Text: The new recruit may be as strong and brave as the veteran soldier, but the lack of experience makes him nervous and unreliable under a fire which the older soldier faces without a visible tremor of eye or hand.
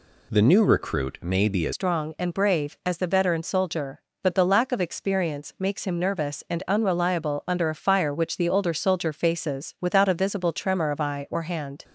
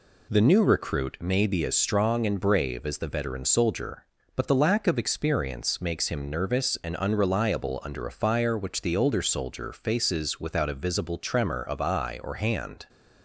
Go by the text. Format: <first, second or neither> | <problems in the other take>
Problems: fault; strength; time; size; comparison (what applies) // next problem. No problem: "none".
second | changes voice at "strong"; from 1.7 s on; 10.1 s long